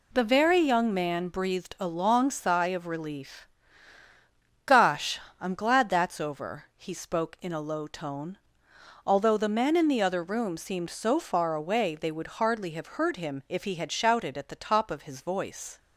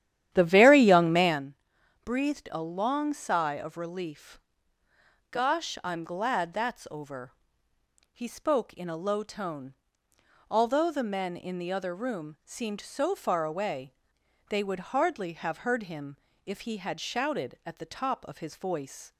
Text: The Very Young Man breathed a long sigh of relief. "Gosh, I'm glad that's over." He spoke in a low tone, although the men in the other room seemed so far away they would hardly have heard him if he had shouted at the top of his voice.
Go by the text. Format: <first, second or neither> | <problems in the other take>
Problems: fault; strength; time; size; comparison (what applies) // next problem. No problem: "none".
first | starts louder than the rest; strong; until 1.5 s; 11 dB // pauses between "Man" and "breathed"; noticeable; at 1.5 s; 0.48 s long // pauses between "away" and "they"; noticeable; at 13.9 s; 0.58 s long // pauses between "him" and "if"; slight; at 16.1 s; 0.30 s long